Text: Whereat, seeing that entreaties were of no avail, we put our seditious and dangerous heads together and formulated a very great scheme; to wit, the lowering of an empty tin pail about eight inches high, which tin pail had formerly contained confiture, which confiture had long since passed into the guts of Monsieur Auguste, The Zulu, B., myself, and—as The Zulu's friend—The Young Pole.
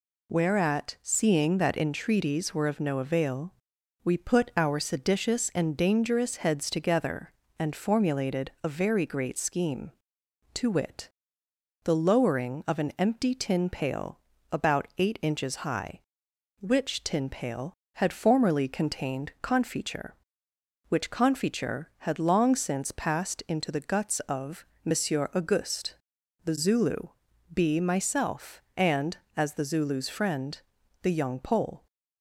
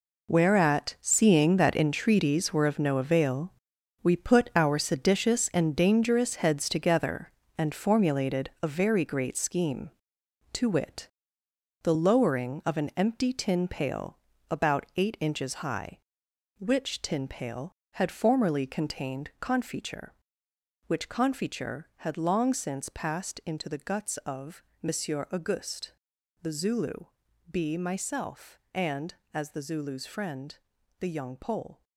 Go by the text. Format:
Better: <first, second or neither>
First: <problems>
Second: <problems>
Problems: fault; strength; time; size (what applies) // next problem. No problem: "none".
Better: first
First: pauses between "pail" and "about"; slight; at 14.1 s; 0.34 s long // pauses between "of" and "Monsieur"; slight; at 24.6 s; 0.18 s long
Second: gets quieter; strong; throughout; 11.5 dB // pauses between "pail" and "about"; slight; at 14.1 s; 0.34 s long // pauses between "of" and "Monsieur"; slight; at 24.6 s; 0.18 s long